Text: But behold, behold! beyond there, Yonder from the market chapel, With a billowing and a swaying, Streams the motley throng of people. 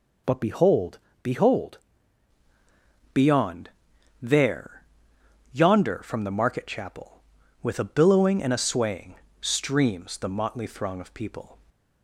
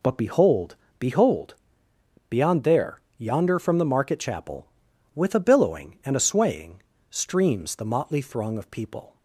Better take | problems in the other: second | changes voice at "beyond"; from 3.1 s on; 8.4 s long // pauses between "beyond" and "there"; noticeable; at 3.6 s; 0.52 s long

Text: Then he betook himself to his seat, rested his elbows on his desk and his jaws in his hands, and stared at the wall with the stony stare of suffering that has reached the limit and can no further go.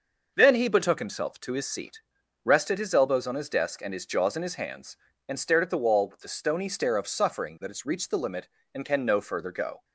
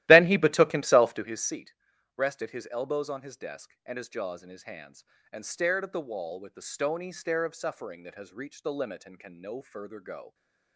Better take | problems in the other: first | starts louder than the rest; strong; until 1.5 s; 15.5 dB

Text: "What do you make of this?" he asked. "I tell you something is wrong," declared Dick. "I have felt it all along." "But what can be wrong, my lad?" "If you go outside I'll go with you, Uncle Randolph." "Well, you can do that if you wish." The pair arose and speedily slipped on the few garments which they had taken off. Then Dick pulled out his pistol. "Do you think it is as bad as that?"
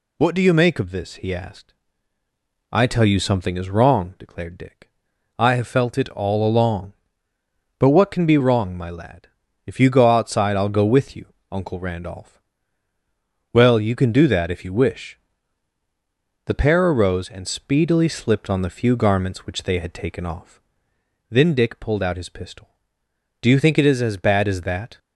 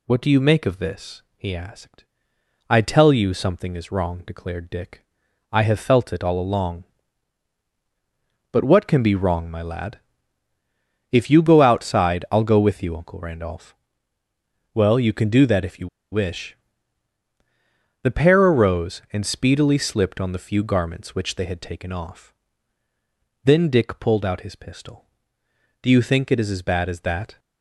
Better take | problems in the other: first | pauses between "you" and "wish"; slight; at 15.8 s; 0.23 s long

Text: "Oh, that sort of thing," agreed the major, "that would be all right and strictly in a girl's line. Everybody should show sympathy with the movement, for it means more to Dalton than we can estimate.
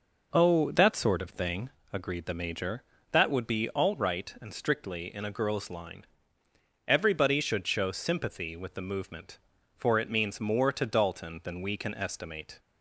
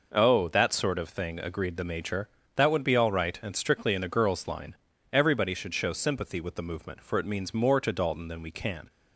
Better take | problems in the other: first | stops before "estimate"; at 8.8 s

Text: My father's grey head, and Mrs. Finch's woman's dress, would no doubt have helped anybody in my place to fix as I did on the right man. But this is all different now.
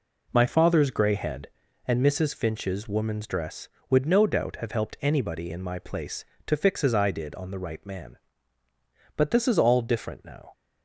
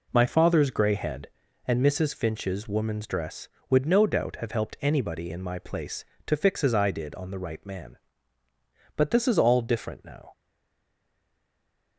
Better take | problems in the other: first | stays silent after the last word; noticeable; from 10.3 s on; 1.6 s long

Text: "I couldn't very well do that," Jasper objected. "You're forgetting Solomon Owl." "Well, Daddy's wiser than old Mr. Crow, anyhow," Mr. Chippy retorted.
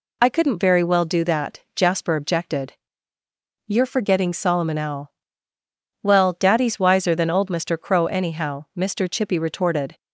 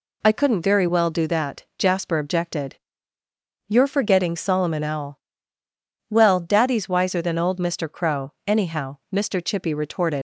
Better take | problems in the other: first | leaves "retorted" unfinished; at 10.1 s; 115 ms

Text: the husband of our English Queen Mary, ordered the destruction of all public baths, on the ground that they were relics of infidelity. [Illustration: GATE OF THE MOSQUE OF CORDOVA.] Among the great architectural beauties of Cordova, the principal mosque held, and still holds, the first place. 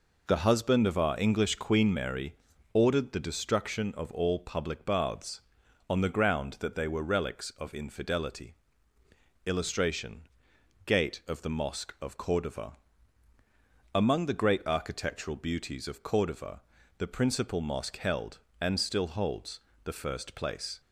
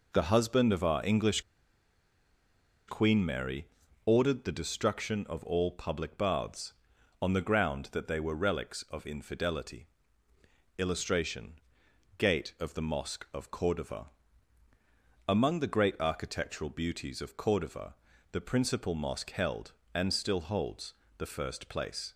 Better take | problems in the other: first | pauses between "English" and "Queen"; strong; at 1.4 s; 1.4 s long

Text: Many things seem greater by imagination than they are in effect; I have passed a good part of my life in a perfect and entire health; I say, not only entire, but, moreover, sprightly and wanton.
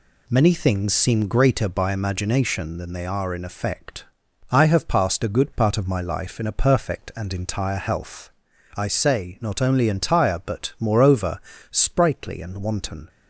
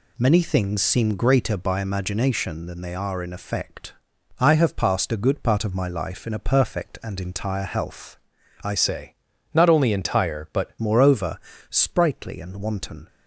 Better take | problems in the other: first | changes voice from "say" to "but"; from 8.7 to 10.7 s; 2.0 s long

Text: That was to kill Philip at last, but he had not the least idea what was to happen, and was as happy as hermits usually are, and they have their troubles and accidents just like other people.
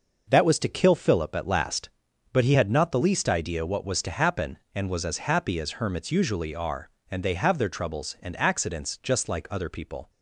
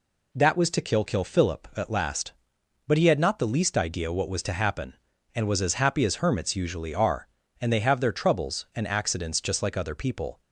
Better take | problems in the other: first | says "kill" twice; at 1.0 s

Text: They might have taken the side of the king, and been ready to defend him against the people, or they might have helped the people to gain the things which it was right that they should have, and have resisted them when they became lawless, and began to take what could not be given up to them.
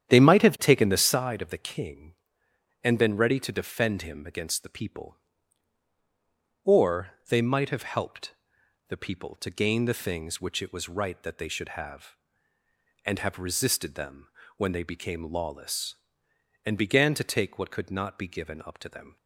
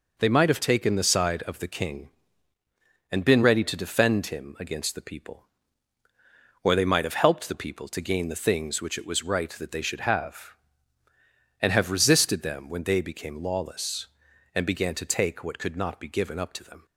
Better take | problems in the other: second | starts louder than the rest; strong; until 1.2 s; 9.5 dB // pauses between "or" and "they"; slight; at 7.1 s; 0.18 s long // pauses between "helped" and "the"; noticeable; at 8.3 s; 0.56 s long // pauses between "them" and "when"; slight; at 14.2 s; 0.28 s long

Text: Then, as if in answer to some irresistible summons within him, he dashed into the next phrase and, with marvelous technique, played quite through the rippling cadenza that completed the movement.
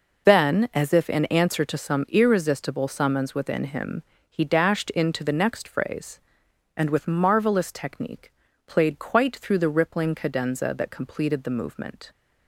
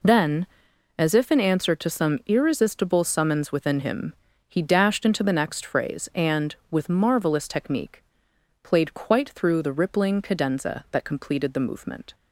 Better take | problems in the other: neither | none

